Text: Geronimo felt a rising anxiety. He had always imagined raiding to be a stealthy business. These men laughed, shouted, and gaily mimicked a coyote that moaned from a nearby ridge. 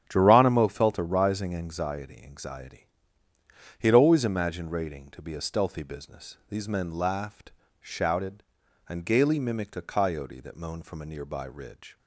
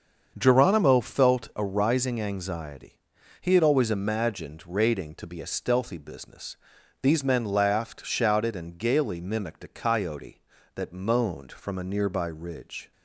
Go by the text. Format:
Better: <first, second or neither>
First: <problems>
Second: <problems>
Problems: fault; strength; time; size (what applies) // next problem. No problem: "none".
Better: second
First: starts louder than the rest; strong; until 1.0 s; 9.5 dB // says "anxiety" twice; at 2.2 s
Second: starts louder than the rest; until 1.3 s; 6.5 dB